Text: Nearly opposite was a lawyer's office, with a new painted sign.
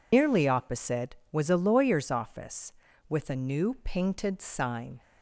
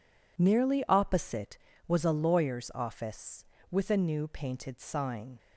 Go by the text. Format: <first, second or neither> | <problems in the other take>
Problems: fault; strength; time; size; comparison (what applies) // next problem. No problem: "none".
second | loses the start of "Nearly"; at 0.1 s; 150 ms